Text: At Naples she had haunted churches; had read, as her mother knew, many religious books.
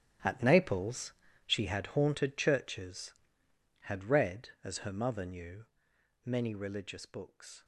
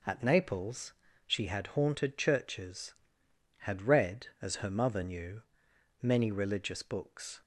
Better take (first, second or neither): second